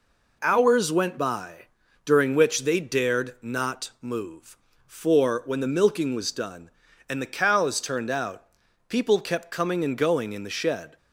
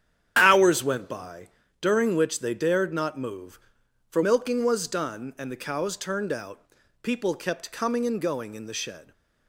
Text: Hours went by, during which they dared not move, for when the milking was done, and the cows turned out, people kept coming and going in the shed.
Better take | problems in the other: first | starts louder than the rest; strong; until 1.4 s; 9 dB // skips "when the"; at 4.2 s

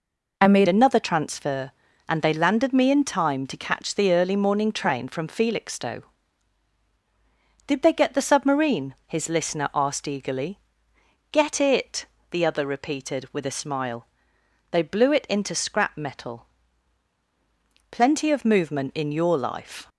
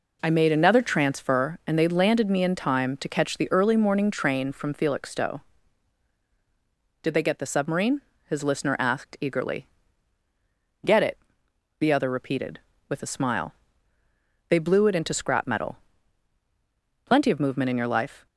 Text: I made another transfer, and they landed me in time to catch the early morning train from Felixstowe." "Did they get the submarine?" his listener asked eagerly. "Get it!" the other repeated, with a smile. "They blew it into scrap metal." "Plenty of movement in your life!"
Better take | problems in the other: second | changes voice at "another"; from 0.6 s on; 19.2 s long

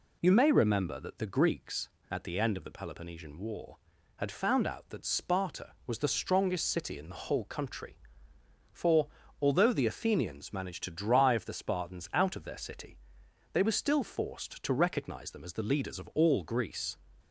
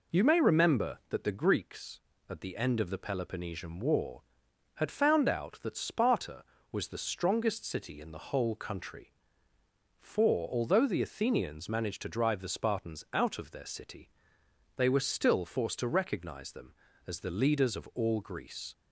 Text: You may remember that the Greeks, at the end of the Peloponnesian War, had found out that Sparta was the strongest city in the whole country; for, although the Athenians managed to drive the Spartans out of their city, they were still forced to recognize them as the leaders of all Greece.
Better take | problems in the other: neither | none

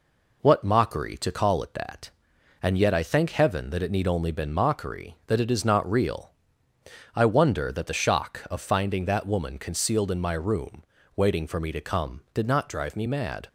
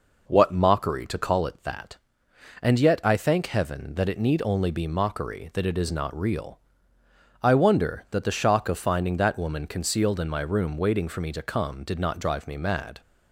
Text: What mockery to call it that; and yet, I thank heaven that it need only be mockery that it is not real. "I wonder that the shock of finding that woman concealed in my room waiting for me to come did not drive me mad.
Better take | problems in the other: second | says "been" for "be"; at 4.3 s // pauses between "room" and "waiting"; slight; at 10.8 s; 0.32 s long

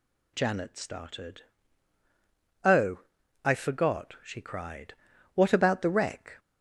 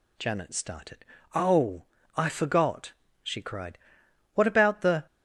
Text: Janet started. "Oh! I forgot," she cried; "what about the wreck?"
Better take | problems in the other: first | stops before "wreck"; at 5.0 s

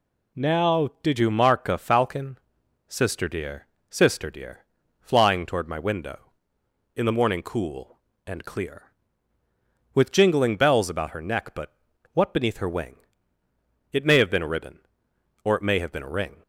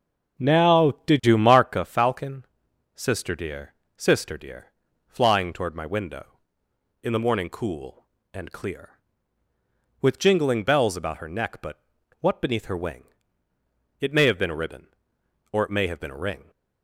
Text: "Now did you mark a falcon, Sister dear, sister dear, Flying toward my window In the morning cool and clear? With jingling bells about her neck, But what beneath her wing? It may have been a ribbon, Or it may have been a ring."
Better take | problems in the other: first | starts louder than the rest; strong; until 1.8 s; 9 dB // pauses between "But" and "what"; at 11.7 s; 0.42 s long; also in the first

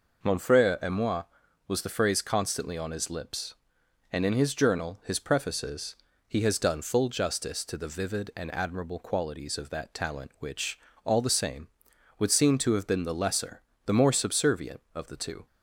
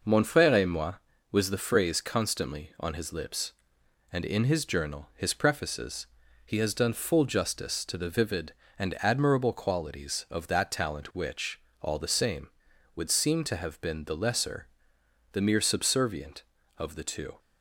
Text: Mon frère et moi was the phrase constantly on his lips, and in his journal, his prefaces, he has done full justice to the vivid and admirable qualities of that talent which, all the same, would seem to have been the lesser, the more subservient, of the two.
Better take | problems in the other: first | says "mere" for "more"; at 15.4 s

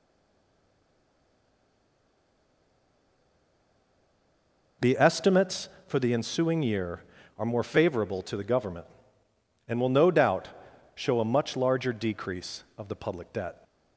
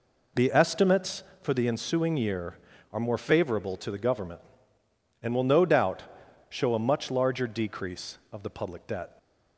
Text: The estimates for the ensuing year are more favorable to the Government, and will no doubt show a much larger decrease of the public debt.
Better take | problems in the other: second | stays silent before the first word; strong; until 4.8 s; 4.8 s long // pauses between "doubt" and "show"; noticeable; at 10.4 s; 0.46 s long; noticeable in the second

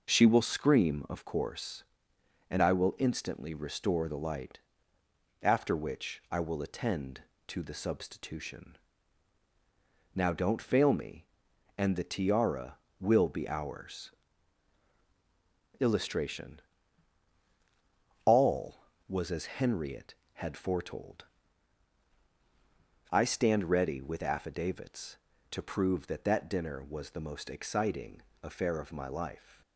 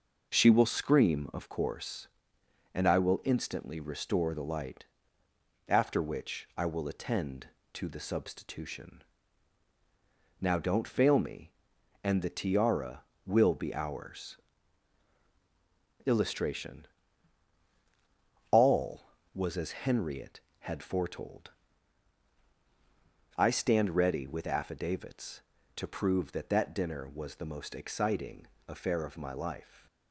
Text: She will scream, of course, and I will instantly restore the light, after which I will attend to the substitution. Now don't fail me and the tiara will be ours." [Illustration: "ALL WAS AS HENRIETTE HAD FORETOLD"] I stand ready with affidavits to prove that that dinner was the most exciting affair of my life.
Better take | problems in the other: neither | pauses between "FORETOLD" and "I"; strong; the same in both // pauses between "exciting" and "affair"; slight; the same in both

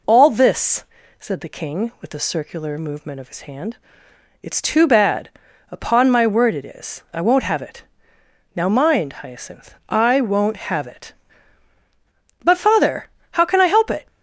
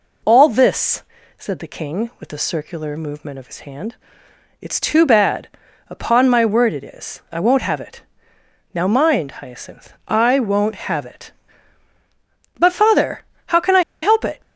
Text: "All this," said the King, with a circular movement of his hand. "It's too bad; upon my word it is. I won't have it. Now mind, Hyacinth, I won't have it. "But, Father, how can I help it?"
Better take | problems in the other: first | pauses between "I" and "help"; slight; at 13.8 s; 0.21 s long

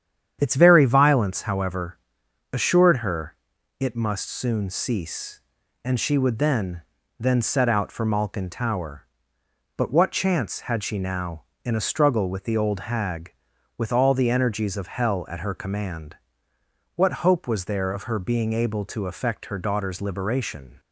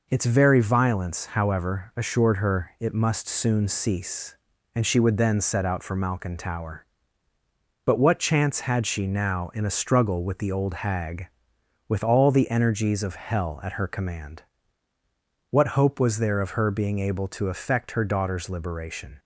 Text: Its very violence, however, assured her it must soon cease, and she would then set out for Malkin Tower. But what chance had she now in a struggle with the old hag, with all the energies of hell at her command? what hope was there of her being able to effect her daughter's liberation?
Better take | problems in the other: second | starts louder than the rest; strong; until 1.4 s; 9 dB // pauses between "her" and "it"; at 3.3 s; 0.42 s long // says "then" twice; at 7.2 s

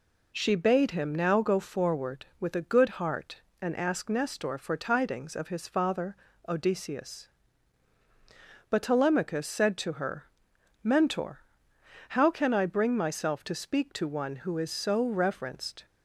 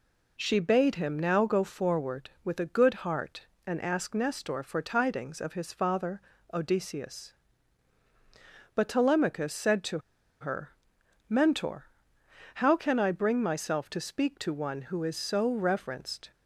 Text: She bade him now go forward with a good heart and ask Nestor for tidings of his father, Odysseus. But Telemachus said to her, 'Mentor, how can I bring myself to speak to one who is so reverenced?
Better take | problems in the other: first | pauses between "to" and "her"; at 9.9 s; 0.41 s long

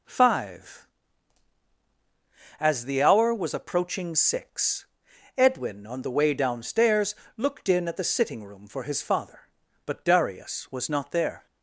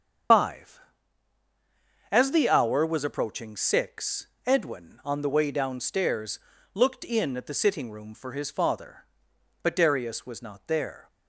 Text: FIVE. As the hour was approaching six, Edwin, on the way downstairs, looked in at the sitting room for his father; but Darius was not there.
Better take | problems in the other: first | loses the start of "FIVE"; at 0.3 s; 115 ms // starts louder than the rest; strong; until 2.6 s; 7.5 dB

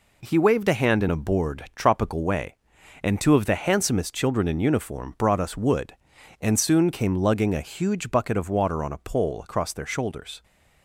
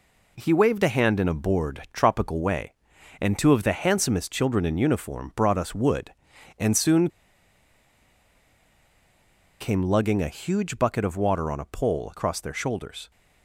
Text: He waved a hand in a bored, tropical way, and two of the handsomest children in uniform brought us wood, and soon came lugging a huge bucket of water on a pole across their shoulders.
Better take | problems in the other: first | pauses between "soon" and "came"; strong; at 7.0 s; 2.5 s long

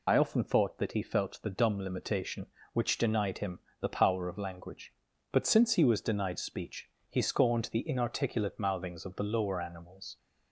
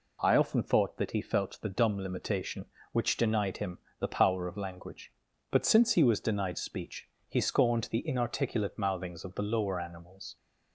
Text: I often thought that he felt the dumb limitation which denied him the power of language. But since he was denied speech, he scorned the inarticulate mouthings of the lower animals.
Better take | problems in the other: second | loses the start of "I"; at 0.0 s; 75 ms // pauses between "him" and "the"; slight; at 3.5 s; 0.22 s long; slight in the second

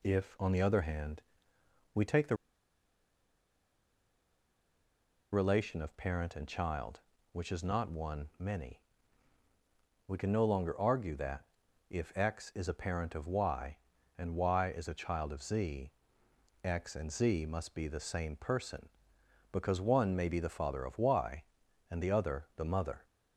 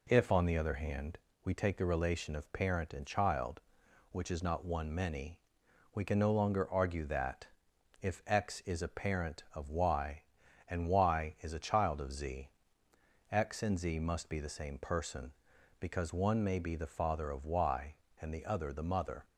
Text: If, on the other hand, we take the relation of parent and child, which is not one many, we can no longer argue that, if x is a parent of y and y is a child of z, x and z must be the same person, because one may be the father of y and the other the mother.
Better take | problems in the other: second | pauses between "the" and "relation"; strong; at 2.3 s; 2.9 s long

